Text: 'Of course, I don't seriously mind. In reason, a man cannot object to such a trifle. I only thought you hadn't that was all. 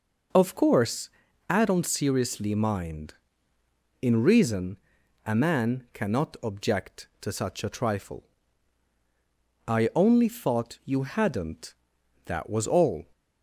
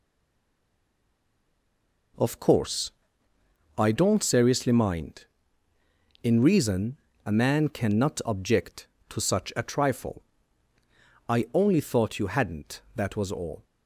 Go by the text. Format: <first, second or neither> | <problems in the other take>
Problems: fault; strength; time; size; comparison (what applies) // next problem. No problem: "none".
first | stays silent before the first word; until 2.1 s; 2.1 s long